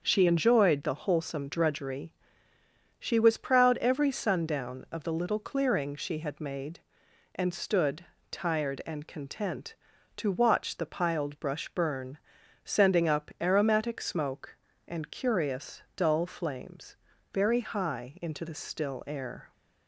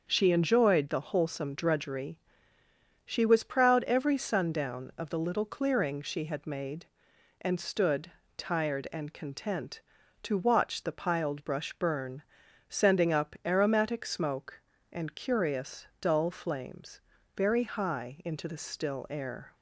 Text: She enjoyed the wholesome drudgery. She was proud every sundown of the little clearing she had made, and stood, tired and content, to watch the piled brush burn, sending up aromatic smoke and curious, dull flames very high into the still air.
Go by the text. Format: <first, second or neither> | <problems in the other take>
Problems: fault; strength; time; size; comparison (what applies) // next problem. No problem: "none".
neither | starts louder than the rest; the same in both // pauses between "flames" and "very"; the same in both